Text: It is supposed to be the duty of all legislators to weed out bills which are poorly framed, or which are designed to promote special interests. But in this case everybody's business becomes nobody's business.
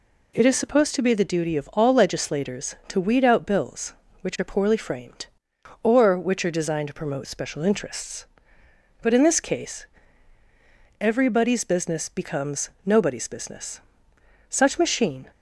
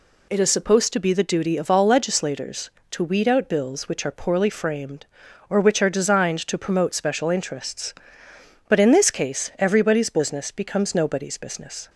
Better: second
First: pauses between "case" and "everybody's"; at 9.8 s; 1.1 s long // goes on to say "Such machine"; noticeable; from 14.5 s on; 0.80 s long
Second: none

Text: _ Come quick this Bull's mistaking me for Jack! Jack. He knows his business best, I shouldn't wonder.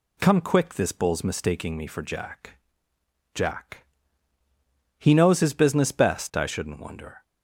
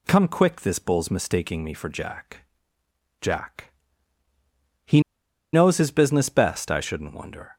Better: first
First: none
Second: pauses between "He" and "knows"; noticeable; at 4.9 s; 0.53 s long

